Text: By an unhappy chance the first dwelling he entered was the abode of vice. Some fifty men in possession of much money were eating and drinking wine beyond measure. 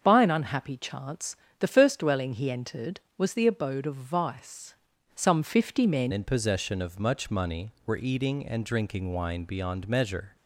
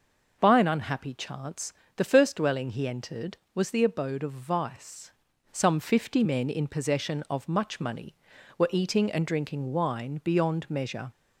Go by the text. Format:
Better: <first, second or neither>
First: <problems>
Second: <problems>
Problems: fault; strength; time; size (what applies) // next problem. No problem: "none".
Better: second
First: starts louder than the rest; until 1.0 s; 6.5 dB // pauses between "chance" and "the"; slight; at 1.3 s; 0.24 s long // changes voice at "in"; from 6.1 s on; 4.2 s long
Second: pauses between "chance" and "the"; slight; at 1.7 s; 0.24 s long